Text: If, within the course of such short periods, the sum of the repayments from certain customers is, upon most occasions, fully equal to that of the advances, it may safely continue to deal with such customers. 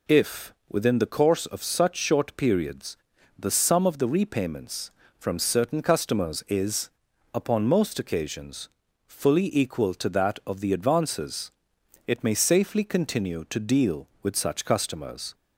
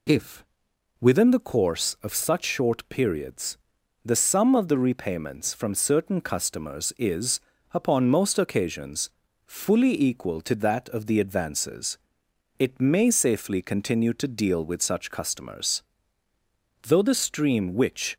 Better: first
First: none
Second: goes on to say "Though the stream which"; from 16.8 s on; 1.3 s long

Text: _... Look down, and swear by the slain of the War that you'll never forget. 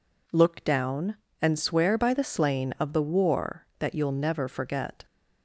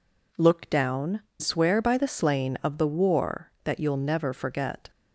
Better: first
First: none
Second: skips "and"; at 1.2 s

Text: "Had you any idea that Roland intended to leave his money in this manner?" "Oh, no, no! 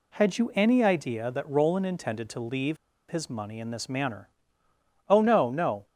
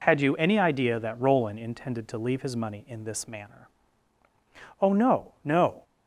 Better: second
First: pauses between "leave" and "his"; slight; at 2.7 s; 0.34 s long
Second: none

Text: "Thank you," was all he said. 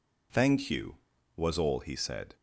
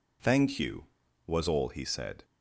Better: neither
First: none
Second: none

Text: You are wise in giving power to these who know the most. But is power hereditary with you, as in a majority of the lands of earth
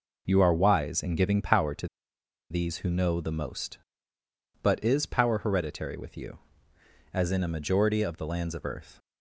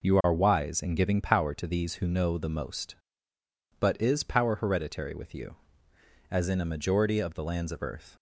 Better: second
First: pauses between "to" and "these"; noticeable; at 1.8 s; 0.64 s long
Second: none

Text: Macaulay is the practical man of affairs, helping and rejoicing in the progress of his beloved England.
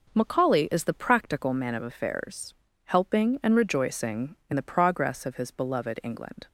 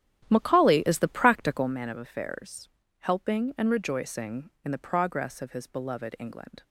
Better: first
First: none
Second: starts louder than the rest; strong; until 1.7 s; 11.5 dB

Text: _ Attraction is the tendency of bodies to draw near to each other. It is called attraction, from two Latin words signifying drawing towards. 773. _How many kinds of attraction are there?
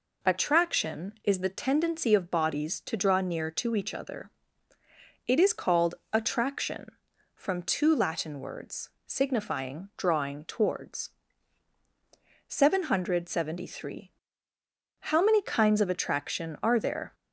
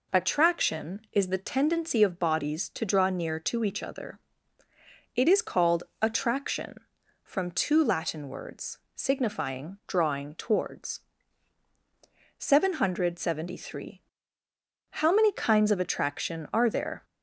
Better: neither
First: pauses between "called" and "attraction"; slight; at 5.9 s; 0.18 s long // pauses between "words" and "signifying"; slight; at 8.8 s; 0.16 s long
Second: pauses between "called" and "attraction"; slight; at 5.8 s; 0.18 s long // pauses between "words" and "signifying"; slight; at 8.7 s; 0.16 s long

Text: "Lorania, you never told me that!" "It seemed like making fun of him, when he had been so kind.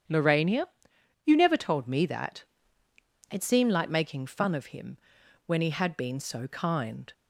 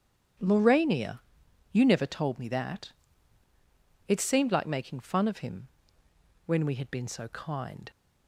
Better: first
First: starts louder than the rest; strong; until 1.6 s; 9 dB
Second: starts louder than the rest; strong; until 1.9 s; 8.5 dB // says "we" for "he"; at 6.6 s

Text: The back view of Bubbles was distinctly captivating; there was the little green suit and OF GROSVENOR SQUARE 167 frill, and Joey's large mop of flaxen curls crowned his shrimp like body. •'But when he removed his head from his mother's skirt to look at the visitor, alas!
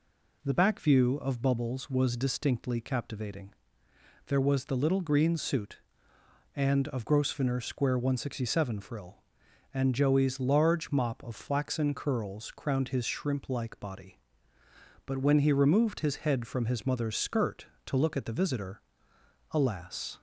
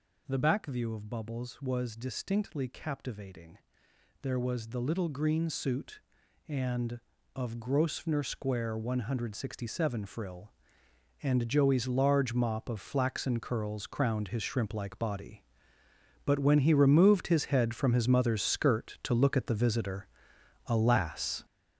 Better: first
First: none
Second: gets louder; strong; throughout; 8 dB

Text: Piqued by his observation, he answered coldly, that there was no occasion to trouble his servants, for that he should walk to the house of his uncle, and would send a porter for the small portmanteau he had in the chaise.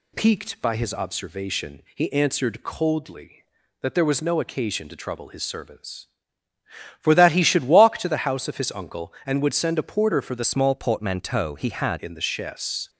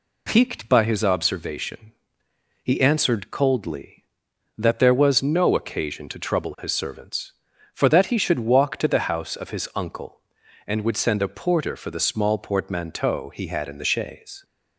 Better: second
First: changes voice from "small" to "had"; from 10.4 to 12.0 s; 1.6 s long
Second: none

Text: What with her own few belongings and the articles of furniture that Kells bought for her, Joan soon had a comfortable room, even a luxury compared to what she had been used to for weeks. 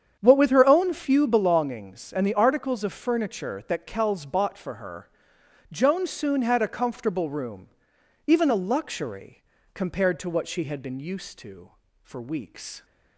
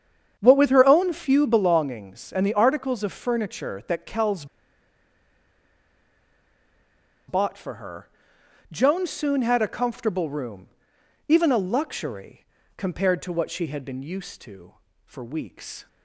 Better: first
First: starts louder than the rest; strong; until 1.2 s; 8 dB // pauses between "luxury" and "compared"; slight; at 9.4 s; 0.30 s long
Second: starts louder than the rest; strong; until 1.4 s; 8 dB // pauses between "Kells" and "bought"; strong; at 4.4 s; 2.8 s long // pauses between "luxury" and "compared"; slight; at 12.4 s; 0.30 s long

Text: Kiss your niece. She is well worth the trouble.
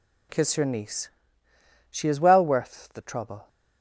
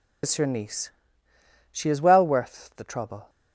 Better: first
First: none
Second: loses the start of "Kiss"; at 0.2 s; 115 ms

